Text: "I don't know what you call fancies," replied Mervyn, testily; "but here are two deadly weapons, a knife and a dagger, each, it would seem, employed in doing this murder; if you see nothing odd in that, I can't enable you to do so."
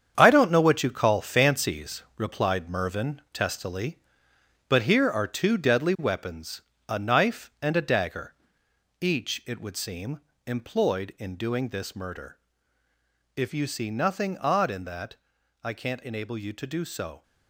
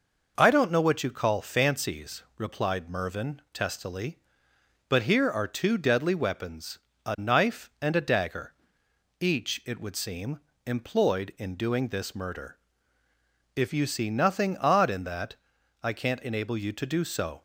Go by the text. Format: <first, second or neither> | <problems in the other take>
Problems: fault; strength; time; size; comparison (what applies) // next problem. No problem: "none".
second | gets quieter; strong; throughout; 9.5 dB